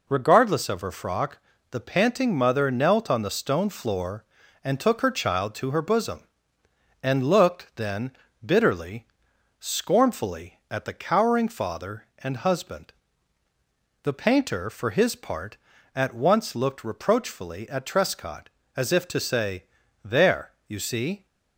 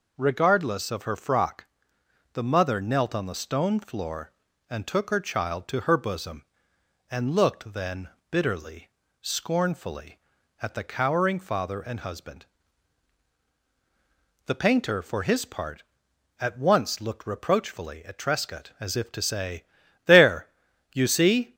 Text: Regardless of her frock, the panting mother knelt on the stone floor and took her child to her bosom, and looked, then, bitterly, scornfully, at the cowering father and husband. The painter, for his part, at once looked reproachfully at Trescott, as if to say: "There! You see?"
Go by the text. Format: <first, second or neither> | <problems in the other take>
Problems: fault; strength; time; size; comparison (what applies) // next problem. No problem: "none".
first | skips "panting"; at 2.4 s